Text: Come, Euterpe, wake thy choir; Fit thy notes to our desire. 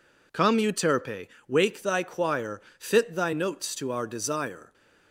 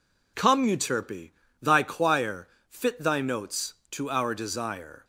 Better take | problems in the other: first | skips "wake"; at 1.4 s

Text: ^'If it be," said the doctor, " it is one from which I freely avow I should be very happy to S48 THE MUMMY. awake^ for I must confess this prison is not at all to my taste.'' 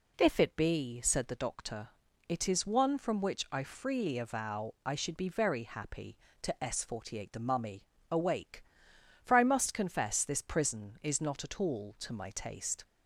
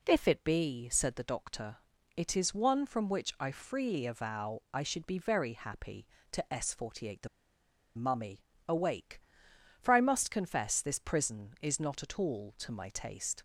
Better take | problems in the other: first | pauses between "THE" and "MUMMY"; noticeable; at 7.2 s; 0.67 s long

